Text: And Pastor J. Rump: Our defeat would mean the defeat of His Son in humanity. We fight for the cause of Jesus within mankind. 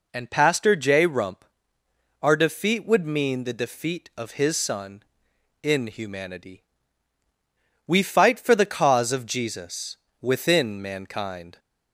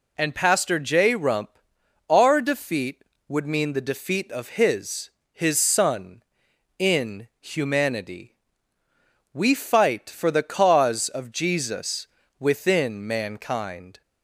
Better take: first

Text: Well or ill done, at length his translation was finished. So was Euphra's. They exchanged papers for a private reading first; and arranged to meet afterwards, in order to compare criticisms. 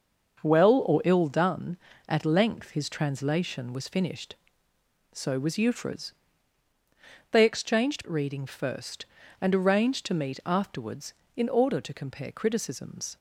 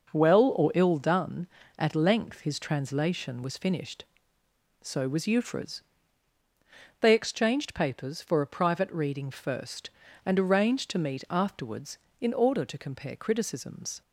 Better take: second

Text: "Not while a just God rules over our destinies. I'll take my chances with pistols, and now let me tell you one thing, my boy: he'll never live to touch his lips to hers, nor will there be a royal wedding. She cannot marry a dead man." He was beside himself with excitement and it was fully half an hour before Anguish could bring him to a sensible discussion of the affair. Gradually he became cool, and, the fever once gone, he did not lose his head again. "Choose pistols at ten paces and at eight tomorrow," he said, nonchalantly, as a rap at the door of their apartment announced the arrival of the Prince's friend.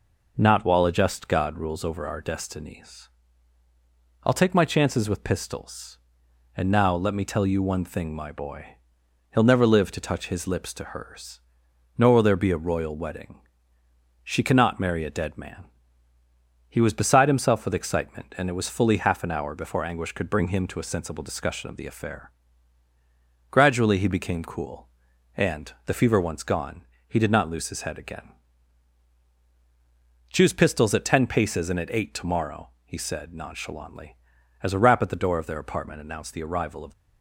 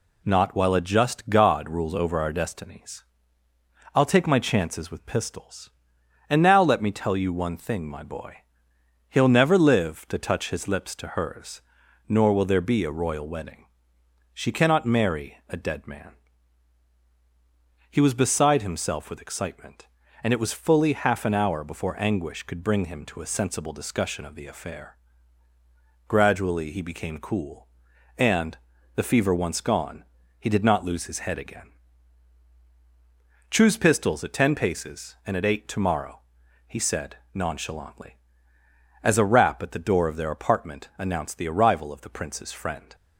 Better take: second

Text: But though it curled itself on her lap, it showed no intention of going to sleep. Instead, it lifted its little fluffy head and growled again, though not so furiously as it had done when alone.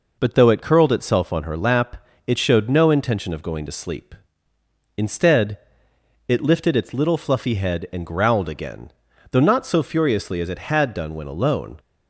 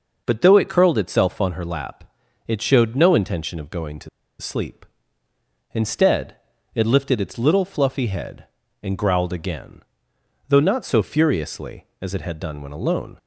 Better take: first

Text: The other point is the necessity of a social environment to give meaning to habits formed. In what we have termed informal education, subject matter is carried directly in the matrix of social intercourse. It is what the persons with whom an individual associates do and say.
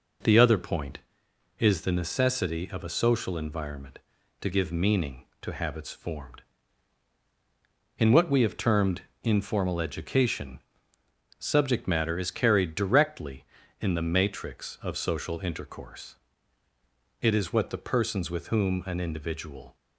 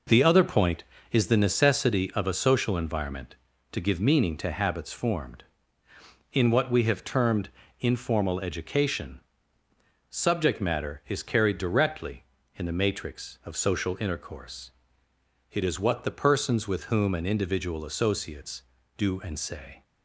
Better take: second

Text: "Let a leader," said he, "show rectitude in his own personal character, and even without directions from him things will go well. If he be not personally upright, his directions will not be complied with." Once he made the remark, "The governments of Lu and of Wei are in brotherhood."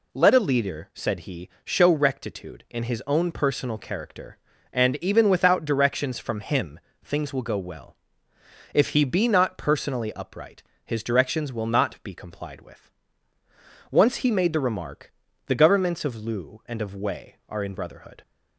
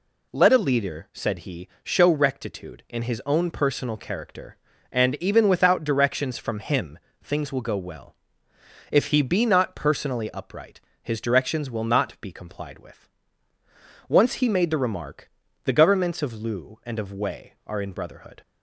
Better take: neither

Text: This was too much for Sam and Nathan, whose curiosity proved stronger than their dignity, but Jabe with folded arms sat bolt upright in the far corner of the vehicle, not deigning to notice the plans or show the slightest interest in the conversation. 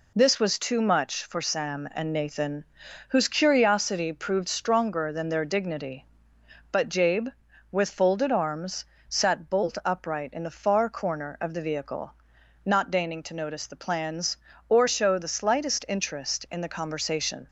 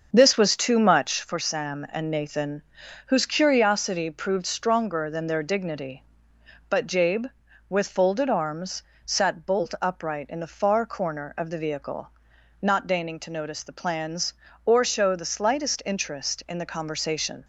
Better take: first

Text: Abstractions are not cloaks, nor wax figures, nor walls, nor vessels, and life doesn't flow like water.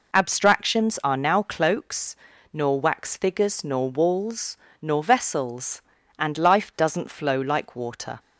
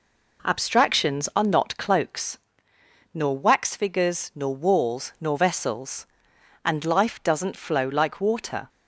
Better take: second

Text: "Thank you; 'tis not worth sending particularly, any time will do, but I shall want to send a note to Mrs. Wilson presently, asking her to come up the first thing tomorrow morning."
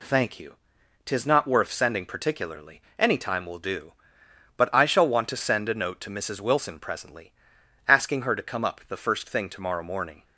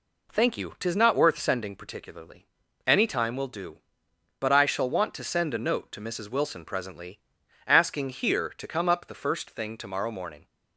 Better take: first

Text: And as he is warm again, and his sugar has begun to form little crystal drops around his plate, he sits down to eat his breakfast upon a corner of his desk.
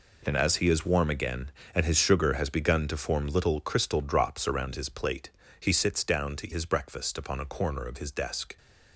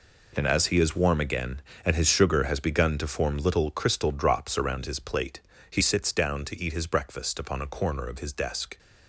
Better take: second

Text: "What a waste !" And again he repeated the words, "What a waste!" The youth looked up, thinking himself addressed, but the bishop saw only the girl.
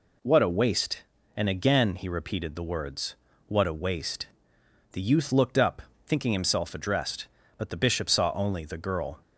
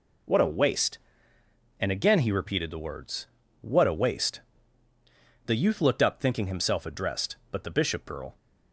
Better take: first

